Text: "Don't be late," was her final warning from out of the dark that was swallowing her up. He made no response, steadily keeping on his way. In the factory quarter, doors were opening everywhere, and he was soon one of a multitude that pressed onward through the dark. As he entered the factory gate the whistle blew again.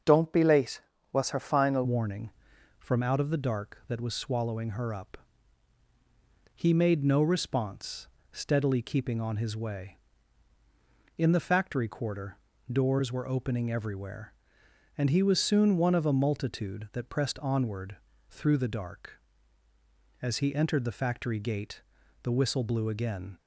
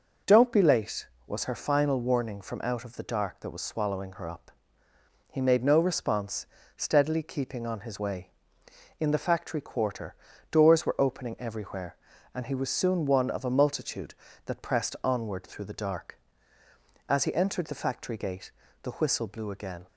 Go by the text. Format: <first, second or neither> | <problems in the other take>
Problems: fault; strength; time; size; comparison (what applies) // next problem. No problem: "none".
second | starts louder than the rest; until 1.3 s; 6.5 dB // changes voice at "warning"; from 1.8 s on; 21.5 s long // pauses between "onward" and "through"; slight; at 17.9 s; 0.34 s long // pauses between "gate" and "the"; at 21.8 s; 0.40 s long; slight in the second